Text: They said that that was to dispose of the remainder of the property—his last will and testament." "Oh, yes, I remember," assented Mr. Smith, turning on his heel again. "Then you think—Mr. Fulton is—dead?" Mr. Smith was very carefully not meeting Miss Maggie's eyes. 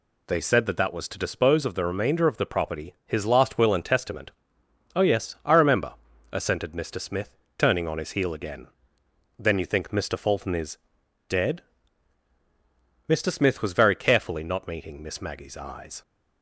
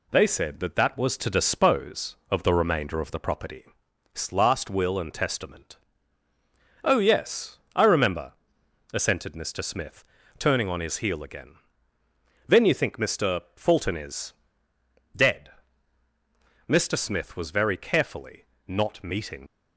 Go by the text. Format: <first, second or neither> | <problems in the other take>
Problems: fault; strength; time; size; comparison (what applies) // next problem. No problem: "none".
first | pauses between "carefully" and "not"; slight; at 18.4 s; 0.20 s long // stops before "Miss Maggie's eyes"; at 19.4 s